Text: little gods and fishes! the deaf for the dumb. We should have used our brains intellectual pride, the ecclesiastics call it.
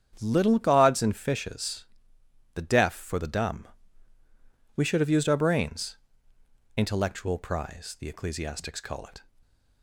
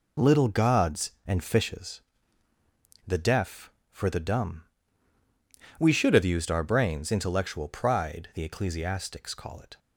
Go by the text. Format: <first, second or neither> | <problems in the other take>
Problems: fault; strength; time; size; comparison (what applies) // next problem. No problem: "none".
second | starts louder than the rest; strong; until 1.2 s; 8.5 dB // pauses between "brains" and "intellectual"; noticeable; at 5.9 s; 0.80 s long // says "prize" for "pride"; at 7.3 s